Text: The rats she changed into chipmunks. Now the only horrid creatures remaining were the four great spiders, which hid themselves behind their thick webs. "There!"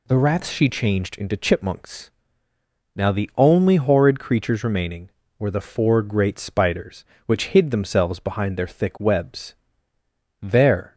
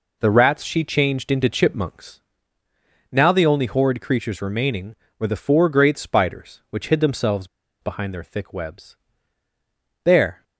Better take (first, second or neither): first